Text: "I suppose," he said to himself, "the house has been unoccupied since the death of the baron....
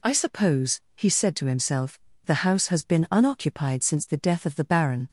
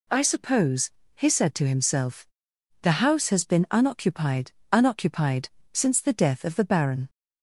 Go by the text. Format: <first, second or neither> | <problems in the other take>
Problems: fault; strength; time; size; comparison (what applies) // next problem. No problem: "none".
first | says "unoccupied" twice; at 4.7 s